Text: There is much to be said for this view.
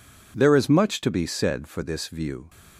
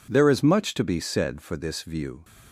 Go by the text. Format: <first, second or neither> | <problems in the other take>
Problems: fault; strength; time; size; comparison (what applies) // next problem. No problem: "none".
neither | none